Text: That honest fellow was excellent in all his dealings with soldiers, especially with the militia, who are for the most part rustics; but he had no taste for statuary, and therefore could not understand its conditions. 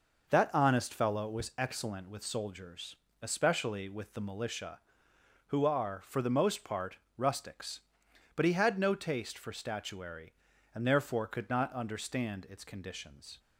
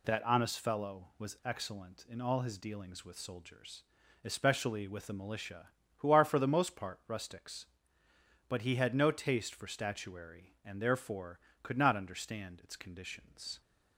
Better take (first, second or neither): second